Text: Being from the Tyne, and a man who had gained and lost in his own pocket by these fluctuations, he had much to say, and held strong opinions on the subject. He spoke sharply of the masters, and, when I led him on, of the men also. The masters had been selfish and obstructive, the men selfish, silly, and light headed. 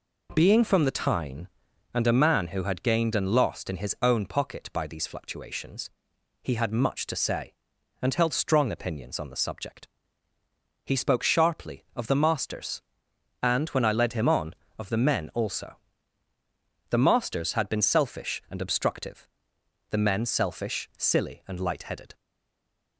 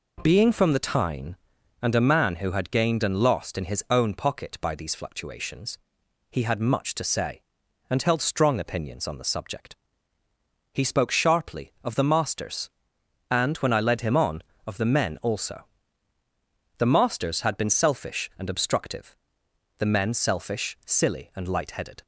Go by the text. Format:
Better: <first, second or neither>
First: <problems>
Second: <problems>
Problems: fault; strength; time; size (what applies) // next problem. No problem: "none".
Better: second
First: stays silent after the last word; slight; from 22.1 s on; 0.8 s long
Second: none